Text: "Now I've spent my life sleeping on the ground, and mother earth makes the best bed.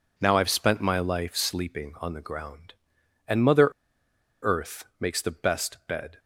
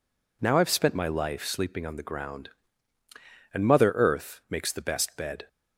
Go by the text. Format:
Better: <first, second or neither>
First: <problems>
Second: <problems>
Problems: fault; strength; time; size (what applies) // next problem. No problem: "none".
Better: second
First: pauses between "mother" and "earth"; noticeable; at 3.6 s; 0.75 s long // pauses between "earth" and "makes"; slight; at 4.8 s; 0.16 s long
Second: none